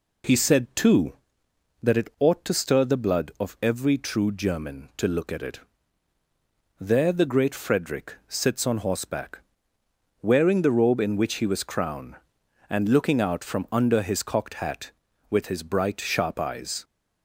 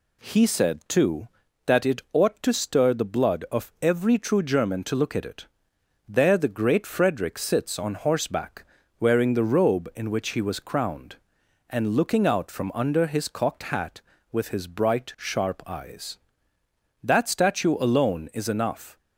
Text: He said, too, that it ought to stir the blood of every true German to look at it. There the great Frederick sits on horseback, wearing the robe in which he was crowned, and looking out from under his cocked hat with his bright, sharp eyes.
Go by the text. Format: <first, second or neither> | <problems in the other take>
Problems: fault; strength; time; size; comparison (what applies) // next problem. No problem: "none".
first | goes on to say "That statue alone is enough"; strong; from 17.0 s on; 1.9 s long